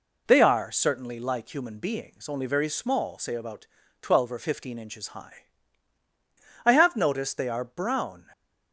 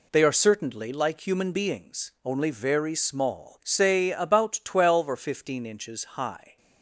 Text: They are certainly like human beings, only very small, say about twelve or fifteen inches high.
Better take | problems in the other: second | pauses between "about" and "twelve"; slight; at 3.6 s; 0.34 s long // goes on to say "I have noticed they are brown"; from 6.6 s on; 1.6 s long

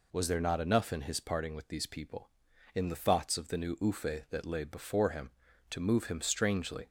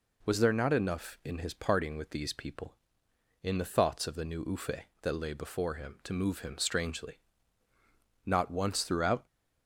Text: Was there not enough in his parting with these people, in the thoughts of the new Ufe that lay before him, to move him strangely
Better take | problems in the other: first | goes on to say "Not once throughout"; noticeable; from 8.2 s on; 1.0 s long

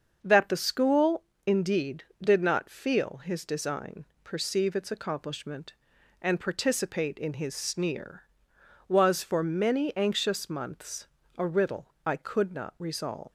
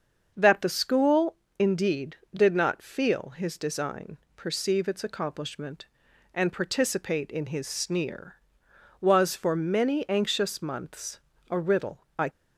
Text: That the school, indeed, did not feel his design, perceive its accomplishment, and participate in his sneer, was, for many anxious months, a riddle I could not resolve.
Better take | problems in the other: first | starts louder than the rest; until 1.3 s; 6.5 dB; also in the first // pauses between "riddle" and "I"; slight; at 11.9 s; 0.18 s long; slight in the first // stops before "could not resolve"; at 12.2 s

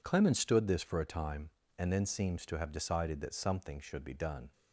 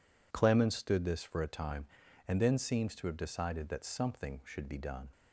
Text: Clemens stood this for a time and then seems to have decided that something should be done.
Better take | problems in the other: neither | none

